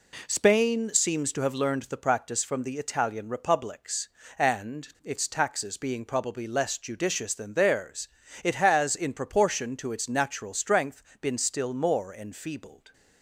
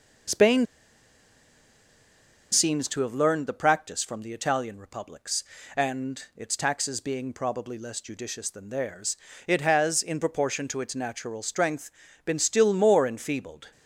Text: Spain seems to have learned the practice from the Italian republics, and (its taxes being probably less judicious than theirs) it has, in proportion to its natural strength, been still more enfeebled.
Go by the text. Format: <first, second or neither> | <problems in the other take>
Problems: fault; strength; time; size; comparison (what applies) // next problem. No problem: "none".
first | pauses between "Spain" and "seems"; strong; at 0.6 s; 1.8 s long